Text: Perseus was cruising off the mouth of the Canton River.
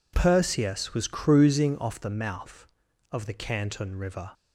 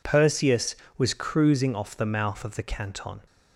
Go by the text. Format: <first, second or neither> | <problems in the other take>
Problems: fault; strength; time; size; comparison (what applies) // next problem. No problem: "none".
first | stops before "River"; at 3.2 s